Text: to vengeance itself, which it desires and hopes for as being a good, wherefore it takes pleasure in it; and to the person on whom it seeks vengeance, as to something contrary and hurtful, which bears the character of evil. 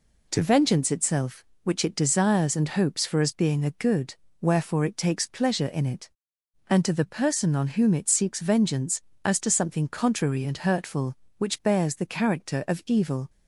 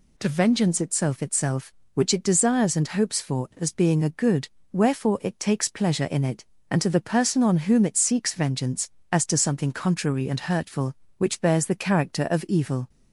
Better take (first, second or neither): first